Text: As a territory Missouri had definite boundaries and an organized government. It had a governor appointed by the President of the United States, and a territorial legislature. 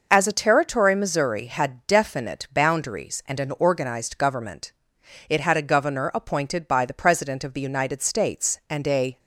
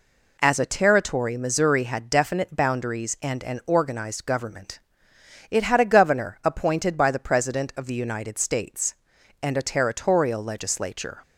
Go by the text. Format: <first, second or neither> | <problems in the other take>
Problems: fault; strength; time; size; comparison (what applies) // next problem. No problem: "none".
second | stops before "territorial legislature"; at 9.1 s